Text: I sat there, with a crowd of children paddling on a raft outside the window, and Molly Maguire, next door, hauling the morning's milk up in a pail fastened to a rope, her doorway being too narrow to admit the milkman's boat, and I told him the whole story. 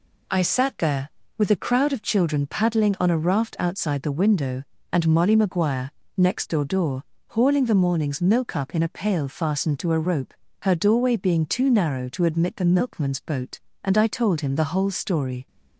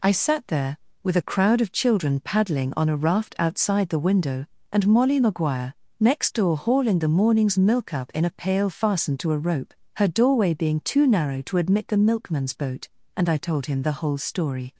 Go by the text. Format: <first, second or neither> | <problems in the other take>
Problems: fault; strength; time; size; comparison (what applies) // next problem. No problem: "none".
second | says "door" twice; at 6.6 s